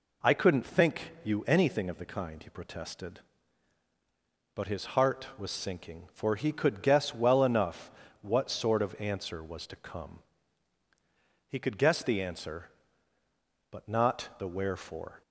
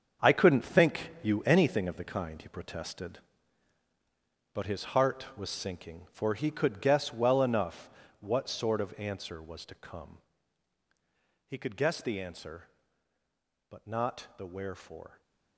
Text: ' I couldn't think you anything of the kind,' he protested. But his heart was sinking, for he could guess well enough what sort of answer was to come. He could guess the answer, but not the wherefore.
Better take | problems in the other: first | gets quieter; strong; throughout; 10.5 dB // pauses between "enough" and "what"; slight; at 7.8 s; 0.32 s long; slight in the first // stays silent after the last word; slight; from 15.0 s on; 0.5 s long

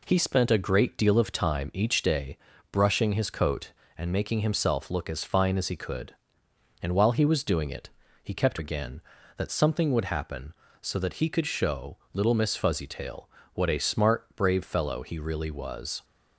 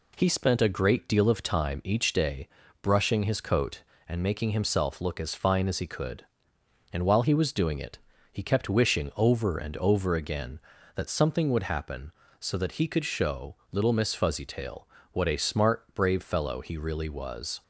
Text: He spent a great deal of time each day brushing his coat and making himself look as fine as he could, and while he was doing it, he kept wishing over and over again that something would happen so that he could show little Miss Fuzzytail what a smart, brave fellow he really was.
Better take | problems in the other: second | pauses between "day" and "brushing"; slight; at 2.3 s; 0.34 s long; slight in the second // skips "wishing over and over"; at 8.5 s // pauses between "show" and "little"; slight; at 11.9 s; 0.16 s long; slight in the second // pauses between "Fuzzytail" and "what"; slight; at 13.2 s; 0.26 s long; slight in the second

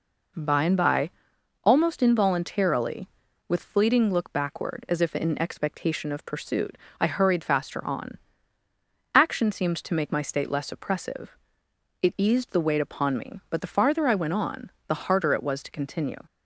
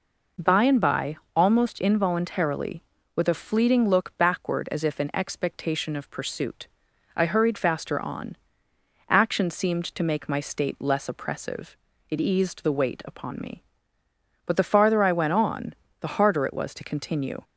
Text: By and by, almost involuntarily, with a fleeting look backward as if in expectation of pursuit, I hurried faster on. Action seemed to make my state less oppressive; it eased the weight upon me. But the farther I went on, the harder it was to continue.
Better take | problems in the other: second | skips "a"; at 3.6 s

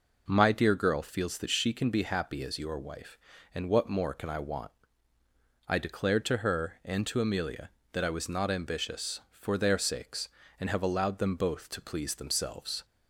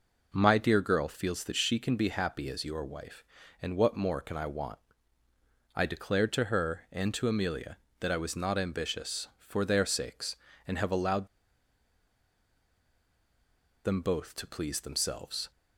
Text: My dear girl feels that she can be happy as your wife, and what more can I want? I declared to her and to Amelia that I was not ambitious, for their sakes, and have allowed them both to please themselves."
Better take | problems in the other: first | pauses between "allowed" and "them"; strong; at 11.2 s; 2.5 s long

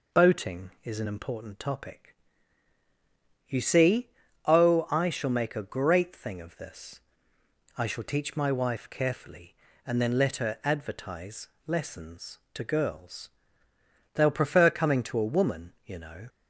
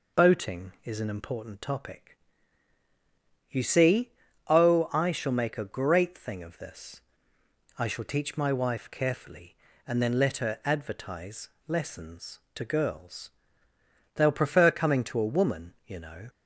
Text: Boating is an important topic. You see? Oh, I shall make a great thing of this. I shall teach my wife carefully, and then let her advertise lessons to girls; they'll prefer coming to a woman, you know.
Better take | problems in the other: neither | pauses between "advertise" and "lessons"; slight; the same in both

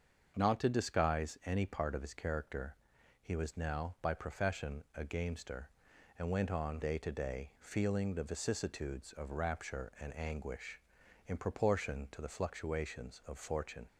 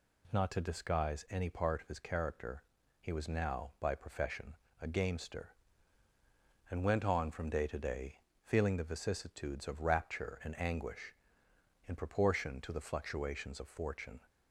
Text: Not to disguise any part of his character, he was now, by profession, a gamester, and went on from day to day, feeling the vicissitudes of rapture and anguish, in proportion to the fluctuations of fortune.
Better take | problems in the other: second | starts louder than the rest; until 1.3 s; 7 dB // skips "from"; at 6.8 s

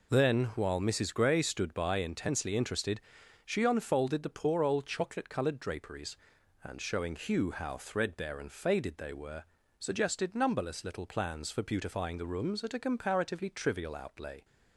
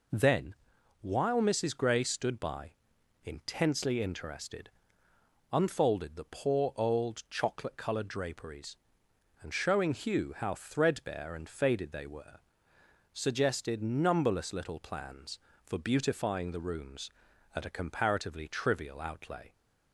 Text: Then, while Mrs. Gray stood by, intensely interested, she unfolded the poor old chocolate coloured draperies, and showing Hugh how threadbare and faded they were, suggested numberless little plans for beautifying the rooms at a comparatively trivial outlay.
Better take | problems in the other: first | skips "she"; at 5.1 s

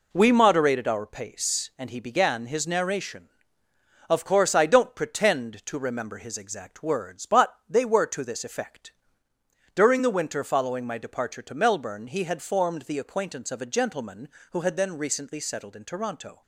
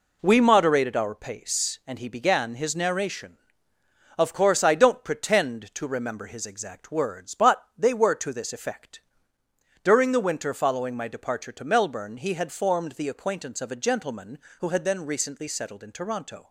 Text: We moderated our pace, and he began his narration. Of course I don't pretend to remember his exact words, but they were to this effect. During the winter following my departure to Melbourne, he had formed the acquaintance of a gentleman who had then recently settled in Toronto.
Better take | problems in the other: neither | none

